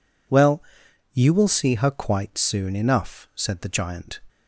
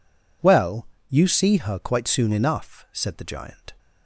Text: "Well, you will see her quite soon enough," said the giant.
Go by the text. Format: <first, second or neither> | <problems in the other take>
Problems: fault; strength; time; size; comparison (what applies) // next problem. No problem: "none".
first | skips "will"; at 1.2 s